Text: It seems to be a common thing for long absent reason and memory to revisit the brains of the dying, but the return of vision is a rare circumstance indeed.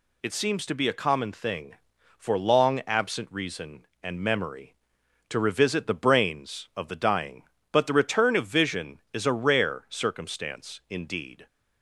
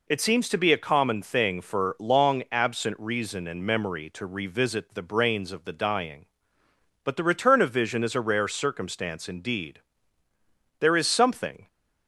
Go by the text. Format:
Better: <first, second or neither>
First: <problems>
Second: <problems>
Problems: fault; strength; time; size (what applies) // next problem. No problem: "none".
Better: first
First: none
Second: goes on to say "There is something"; noticeable; from 10.7 s on; 0.88 s long